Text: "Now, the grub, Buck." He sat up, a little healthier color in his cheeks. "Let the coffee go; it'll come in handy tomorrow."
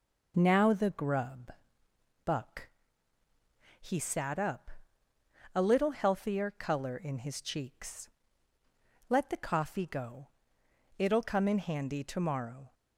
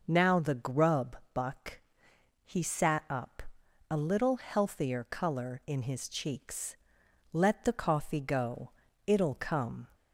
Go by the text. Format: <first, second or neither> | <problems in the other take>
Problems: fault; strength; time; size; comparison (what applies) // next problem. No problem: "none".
first | stops before "in handy tomorrow"; at 9.9 s